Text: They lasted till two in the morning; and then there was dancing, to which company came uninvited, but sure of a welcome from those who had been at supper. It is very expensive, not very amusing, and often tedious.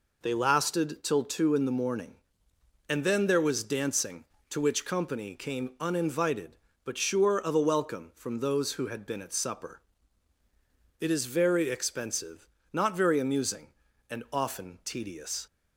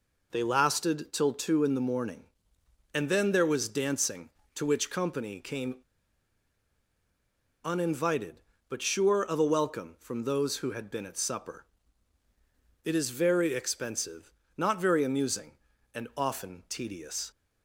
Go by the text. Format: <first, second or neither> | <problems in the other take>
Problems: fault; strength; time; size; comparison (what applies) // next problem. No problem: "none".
first | pauses between "came" and "uninvited"; strong; at 5.7 s; 1.8 s long